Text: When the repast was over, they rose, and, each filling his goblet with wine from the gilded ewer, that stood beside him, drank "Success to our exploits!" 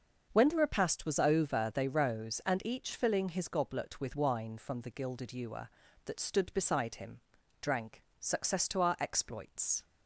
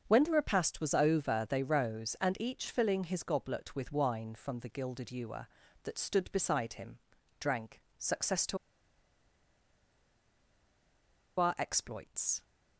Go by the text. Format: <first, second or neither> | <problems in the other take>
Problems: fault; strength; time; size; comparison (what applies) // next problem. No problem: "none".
first | starts louder than the rest; until 1.0 s; 6.5 dB; also in the first // pauses between "drank" and "Success"; slight; at 7.8 s; 0.16 s long; slight in the first // pauses between "to" and "our"; strong; at 8.5 s; 2.8 s long